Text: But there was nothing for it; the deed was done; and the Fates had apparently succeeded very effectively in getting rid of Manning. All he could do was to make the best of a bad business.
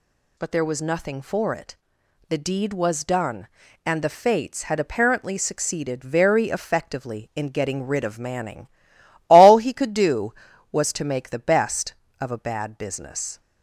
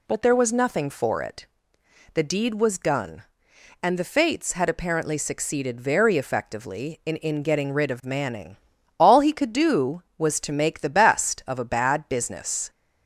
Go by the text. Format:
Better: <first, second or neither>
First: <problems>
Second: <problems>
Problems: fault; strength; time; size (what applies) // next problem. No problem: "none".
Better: first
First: none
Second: says "in" twice; at 7.1 s